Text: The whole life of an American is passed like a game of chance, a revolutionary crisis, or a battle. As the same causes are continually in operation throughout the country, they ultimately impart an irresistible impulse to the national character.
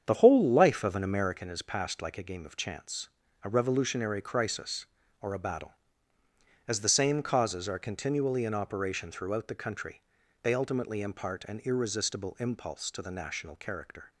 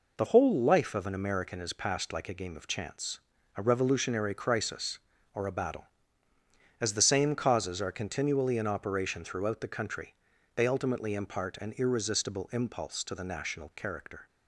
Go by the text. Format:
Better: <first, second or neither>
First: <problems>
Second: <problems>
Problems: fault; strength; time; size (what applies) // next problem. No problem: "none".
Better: second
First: starts louder than the rest; strong; until 1.4 s; 8 dB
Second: none